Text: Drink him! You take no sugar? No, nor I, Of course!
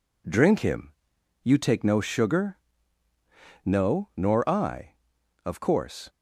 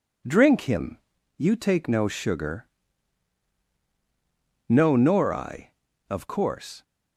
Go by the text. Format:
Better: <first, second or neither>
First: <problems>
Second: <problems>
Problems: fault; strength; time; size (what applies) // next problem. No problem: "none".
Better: neither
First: none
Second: none